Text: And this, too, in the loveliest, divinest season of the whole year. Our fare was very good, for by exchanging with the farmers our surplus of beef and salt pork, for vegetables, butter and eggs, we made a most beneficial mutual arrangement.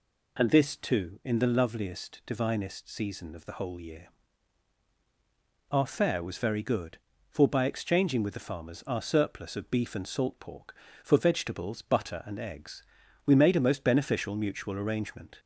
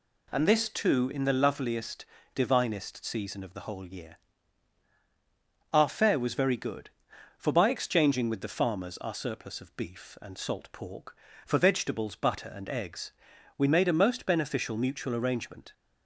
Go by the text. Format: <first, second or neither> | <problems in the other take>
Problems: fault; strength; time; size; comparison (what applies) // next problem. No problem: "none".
neither | none